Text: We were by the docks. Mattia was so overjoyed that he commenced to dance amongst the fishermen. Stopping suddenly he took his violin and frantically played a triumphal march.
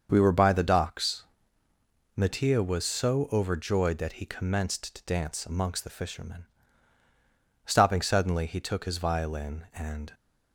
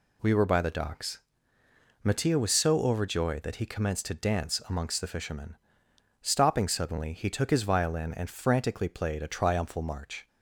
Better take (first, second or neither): second